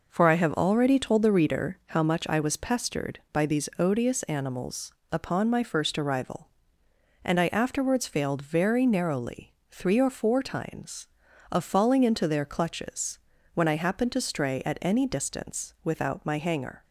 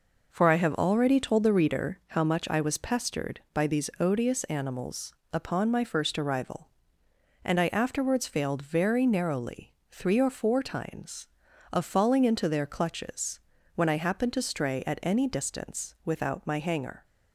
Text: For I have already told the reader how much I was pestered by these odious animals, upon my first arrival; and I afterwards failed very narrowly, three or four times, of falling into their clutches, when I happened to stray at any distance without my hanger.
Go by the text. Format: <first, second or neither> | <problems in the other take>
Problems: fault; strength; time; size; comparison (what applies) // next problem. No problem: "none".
neither | none